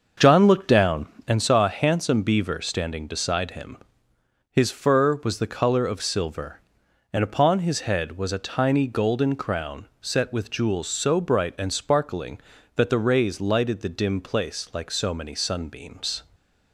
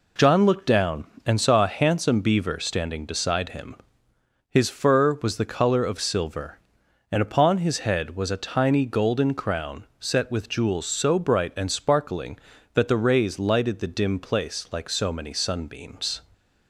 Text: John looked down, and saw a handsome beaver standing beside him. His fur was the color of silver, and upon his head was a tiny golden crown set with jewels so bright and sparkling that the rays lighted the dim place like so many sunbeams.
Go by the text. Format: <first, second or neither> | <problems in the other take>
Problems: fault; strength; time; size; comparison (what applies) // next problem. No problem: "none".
second | starts louder than the rest; until 1.3 s; 6.5 dB // stays silent after the last word; slight; from 16.2 s on; 0.5 s long